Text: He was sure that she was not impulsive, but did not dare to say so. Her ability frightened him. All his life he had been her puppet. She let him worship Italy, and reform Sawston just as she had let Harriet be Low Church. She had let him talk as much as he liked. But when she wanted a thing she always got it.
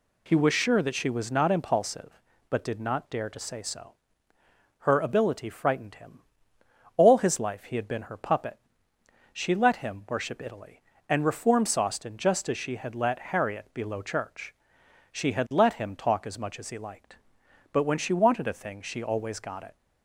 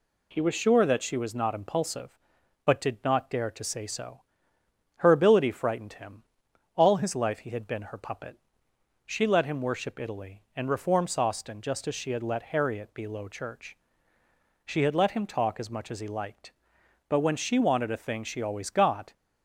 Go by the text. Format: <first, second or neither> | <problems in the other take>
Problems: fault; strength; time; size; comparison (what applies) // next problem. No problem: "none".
first | stops before "it"; at 19.1 s